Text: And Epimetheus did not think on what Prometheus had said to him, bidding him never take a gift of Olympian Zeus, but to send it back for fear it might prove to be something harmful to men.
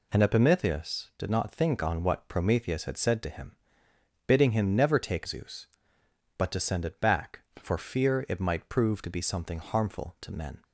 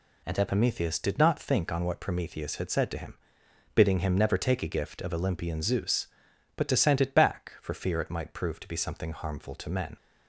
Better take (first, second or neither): second